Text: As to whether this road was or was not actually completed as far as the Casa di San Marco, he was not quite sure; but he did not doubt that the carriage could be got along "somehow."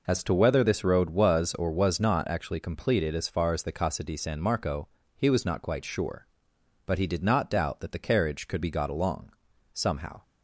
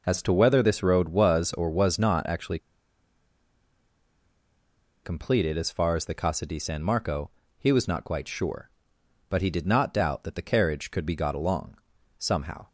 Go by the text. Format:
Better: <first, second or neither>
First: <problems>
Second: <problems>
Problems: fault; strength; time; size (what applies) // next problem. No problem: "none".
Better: first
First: pauses between "along" and "somehow"; at 9.3 s; 0.42 s long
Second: pauses between "actually" and "completed"; strong; at 2.5 s; 2.4 s long // pauses between "along" and "somehow"; at 11.7 s; 0.42 s long